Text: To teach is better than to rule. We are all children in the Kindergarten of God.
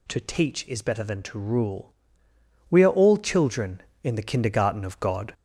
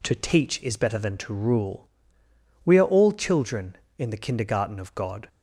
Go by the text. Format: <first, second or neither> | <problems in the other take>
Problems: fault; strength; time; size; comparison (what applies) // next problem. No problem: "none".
second | gets louder; noticeable; throughout; 4.5 dB